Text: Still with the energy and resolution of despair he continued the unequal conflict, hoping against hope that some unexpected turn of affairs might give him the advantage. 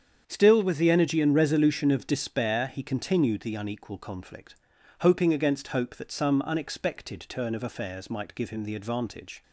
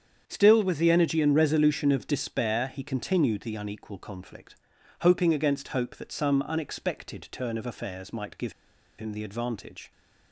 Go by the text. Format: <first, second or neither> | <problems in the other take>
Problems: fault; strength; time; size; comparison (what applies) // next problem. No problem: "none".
first | starts louder than the rest; strong; until 1.2 s; 8 dB; strong in the first // pauses between "give" and "him"; noticeable; at 8.5 s; 0.46 s long